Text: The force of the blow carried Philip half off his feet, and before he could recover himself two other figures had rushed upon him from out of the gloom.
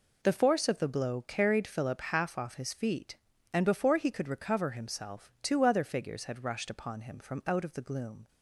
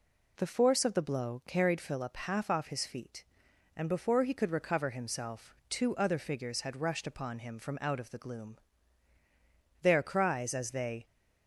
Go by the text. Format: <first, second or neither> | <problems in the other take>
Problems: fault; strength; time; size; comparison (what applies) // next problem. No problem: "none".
first | goes on to say "Their cries as they"; noticeable; from 9.8 s on; 1.2 s long